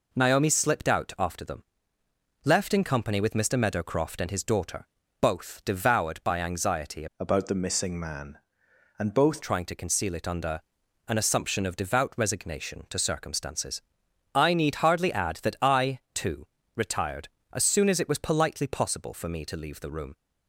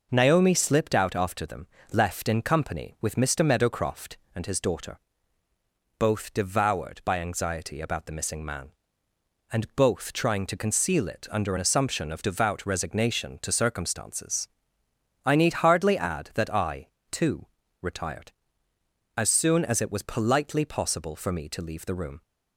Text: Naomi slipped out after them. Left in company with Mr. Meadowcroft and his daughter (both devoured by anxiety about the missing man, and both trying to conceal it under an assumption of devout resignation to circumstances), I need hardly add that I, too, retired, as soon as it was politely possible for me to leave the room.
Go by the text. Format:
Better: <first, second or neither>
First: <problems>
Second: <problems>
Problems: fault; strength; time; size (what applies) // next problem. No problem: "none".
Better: second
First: changes voice from "about" to "both"; from 7.1 to 9.4 s; 2.3 s long // pauses between "under" and "an"; noticeable; at 10.6 s; 0.46 s long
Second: none